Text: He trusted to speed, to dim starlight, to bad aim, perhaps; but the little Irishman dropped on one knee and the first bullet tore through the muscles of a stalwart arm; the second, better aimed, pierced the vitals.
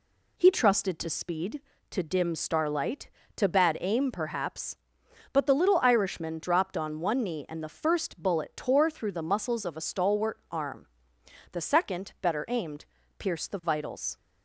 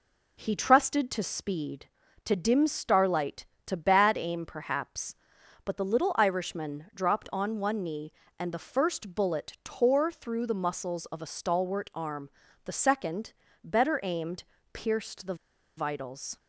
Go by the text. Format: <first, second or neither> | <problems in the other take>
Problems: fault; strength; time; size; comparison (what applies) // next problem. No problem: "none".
first | pauses between "the" and "vitals"; at 15.3 s; 0.42 s long